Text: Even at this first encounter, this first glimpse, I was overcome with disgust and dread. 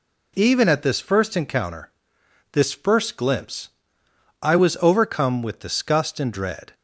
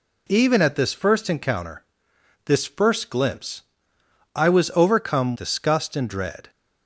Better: first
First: none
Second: skips "with"; at 5.3 s

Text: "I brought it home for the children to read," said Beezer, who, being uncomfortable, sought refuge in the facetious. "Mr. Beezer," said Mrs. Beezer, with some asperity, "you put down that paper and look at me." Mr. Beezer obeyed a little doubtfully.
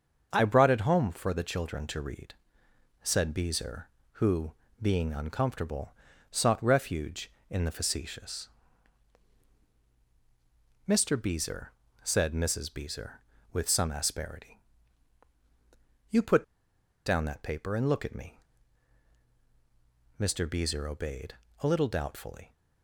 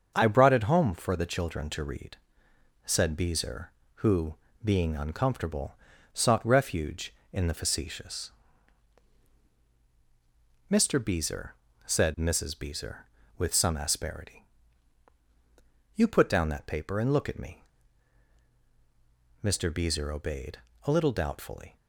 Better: second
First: starts louder than the rest; until 1.3 s; 6.5 dB // pauses between "put" and "down"; noticeable; at 16.4 s; 0.61 s long // pauses between "obeyed" and "a"; slight; at 21.3 s; 0.26 s long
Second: starts louder than the rest; until 1.1 s; 6.5 dB // pauses between "obeyed" and "a"; slight; at 20.5 s; 0.26 s long

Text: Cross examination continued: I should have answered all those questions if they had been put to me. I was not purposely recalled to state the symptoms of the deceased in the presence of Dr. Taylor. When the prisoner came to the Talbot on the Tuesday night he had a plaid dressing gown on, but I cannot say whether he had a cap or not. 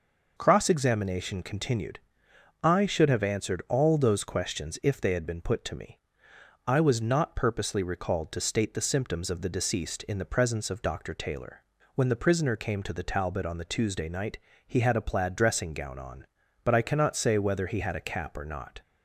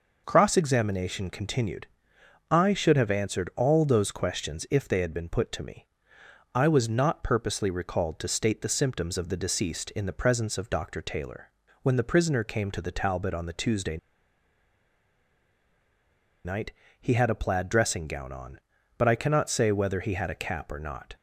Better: first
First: pauses between "night" and "he"; slight; at 14.3 s; 0.30 s long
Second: pauses between "Tuesday" and "night"; strong; at 13.9 s; 2.4 s long // pauses between "night" and "he"; slight; at 16.7 s; 0.30 s long

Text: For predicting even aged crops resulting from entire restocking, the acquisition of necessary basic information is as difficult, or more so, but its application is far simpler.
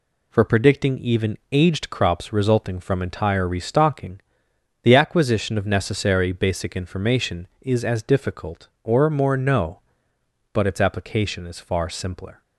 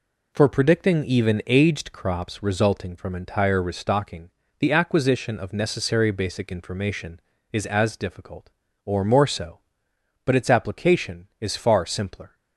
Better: second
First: says "no" for "so"; at 9.3 s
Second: none

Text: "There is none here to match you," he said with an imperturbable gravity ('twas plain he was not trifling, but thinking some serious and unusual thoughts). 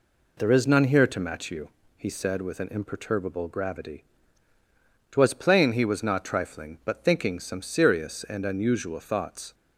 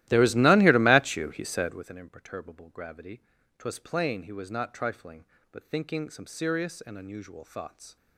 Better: first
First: none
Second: starts louder than the rest; strong; until 1.9 s; 15.5 dB

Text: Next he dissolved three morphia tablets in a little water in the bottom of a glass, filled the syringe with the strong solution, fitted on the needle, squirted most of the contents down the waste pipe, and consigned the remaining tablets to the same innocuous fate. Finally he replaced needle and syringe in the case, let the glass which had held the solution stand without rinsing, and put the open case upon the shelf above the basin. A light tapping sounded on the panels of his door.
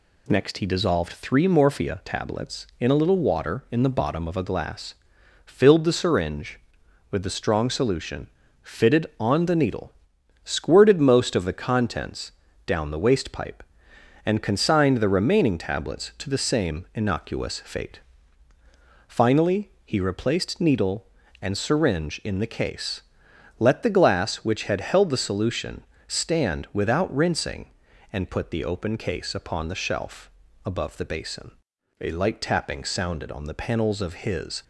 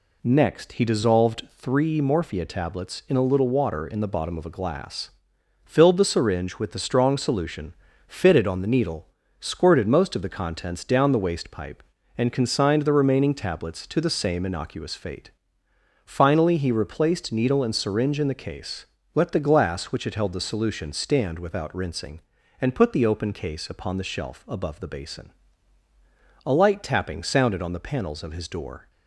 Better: second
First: pauses between "contents" and "down"; slight; at 12.3 s; 0.32 s long // pauses between "Finally" and "he"; slight; at 19.6 s; 0.16 s long // pauses between "solution" and "stand"; slight; at 25.8 s; 0.24 s long // pauses between "shelf" and "above"; slight; at 30.2 s; 0.34 s long // stops before "door"; at 34.6 s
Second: none

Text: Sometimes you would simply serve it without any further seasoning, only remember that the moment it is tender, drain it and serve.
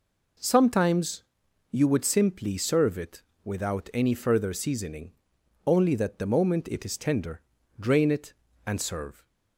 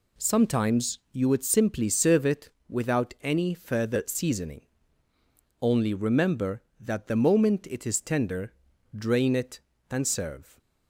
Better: second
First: pauses between "Sometimes" and "you"; noticeable; at 1.2 s; 0.48 s long // pauses between "it" and "without"; slight; at 3.2 s; 0.20 s long // skips "remember"; at 5.9 s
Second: pauses between "it" and "without"; slight; at 2.4 s; 0.20 s long

